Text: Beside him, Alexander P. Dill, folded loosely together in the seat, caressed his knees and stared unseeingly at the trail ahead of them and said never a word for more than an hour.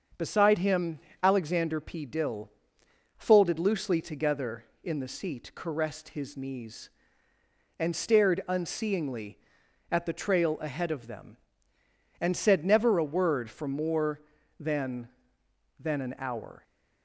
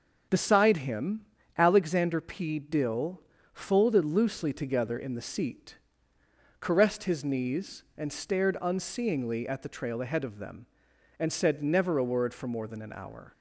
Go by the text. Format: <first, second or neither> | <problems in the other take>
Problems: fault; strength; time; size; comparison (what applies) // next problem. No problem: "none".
second | starts louder than the rest; until 1.4 s; 6.5 dB; also in the second // says "than" twice; at 15.7 s